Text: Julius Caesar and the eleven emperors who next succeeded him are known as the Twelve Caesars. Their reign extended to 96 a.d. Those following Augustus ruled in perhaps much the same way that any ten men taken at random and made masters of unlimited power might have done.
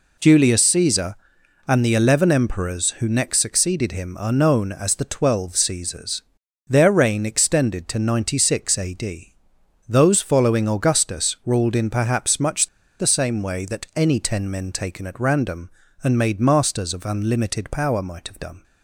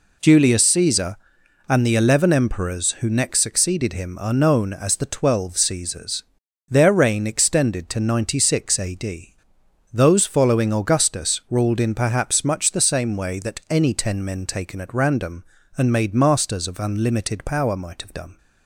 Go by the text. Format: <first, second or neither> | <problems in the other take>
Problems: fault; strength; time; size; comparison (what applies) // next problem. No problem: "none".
second | pauses between "much" and "the"; slight; at 12.6 s; 0.33 s long